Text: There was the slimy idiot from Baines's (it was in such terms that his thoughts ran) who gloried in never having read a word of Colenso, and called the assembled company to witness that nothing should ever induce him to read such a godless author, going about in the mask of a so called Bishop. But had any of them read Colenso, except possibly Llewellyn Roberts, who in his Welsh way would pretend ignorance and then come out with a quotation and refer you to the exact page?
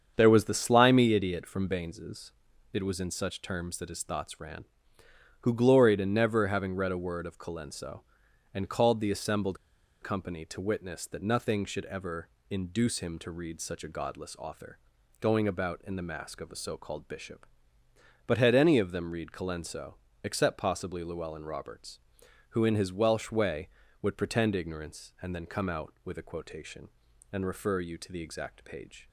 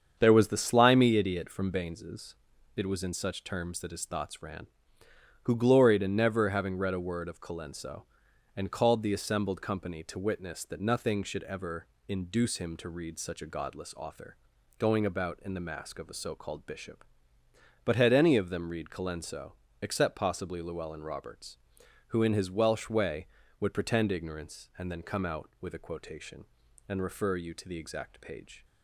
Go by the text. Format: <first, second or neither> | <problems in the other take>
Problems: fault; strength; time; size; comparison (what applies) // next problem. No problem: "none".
second | starts louder than the rest; strong; until 1.1 s; 7.5 dB; strong in the second // pauses between "assembled" and "company"; at 9.5 s; 0.44 s long // pauses between "ever" and "induce"; slight; at 12.2 s; 0.22 s long; slight in the second